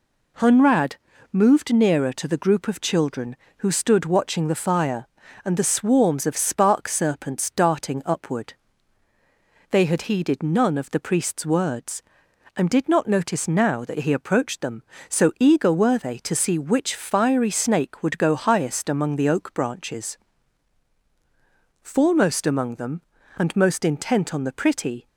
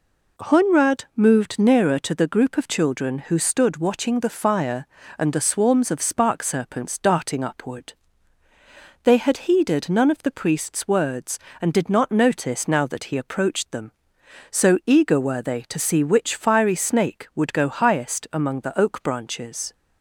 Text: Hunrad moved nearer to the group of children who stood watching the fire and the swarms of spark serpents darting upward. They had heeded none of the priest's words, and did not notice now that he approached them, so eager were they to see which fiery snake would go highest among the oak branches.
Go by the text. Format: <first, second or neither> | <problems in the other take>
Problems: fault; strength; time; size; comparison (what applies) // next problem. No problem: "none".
second | pauses between "Hunrad" and "moved"; slight; at 0.9 s; 0.34 s long // goes on to say "Foremost among them and most intent on the pretty"; strong; from 21.8 s on; 3.2 s long